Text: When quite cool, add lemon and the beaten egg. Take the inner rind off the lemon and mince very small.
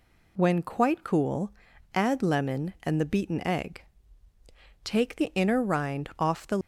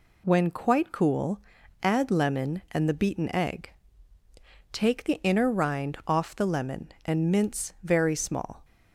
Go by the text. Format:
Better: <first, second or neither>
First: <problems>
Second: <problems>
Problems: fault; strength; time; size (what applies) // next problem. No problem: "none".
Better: second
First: stops before "lemon and mince very small"; at 6.6 s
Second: none